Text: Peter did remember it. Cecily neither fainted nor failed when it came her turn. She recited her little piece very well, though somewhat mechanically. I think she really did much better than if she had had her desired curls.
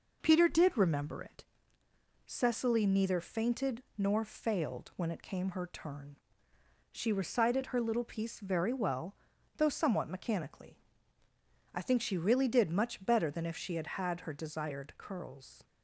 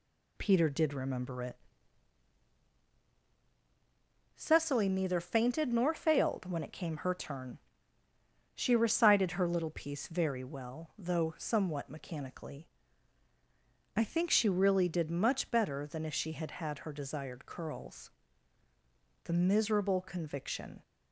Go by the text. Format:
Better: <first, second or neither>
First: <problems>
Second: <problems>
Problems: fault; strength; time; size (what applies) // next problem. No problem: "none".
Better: first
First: none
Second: goes on to say "The miserable conviction"; from 19.2 s on; 1.5 s long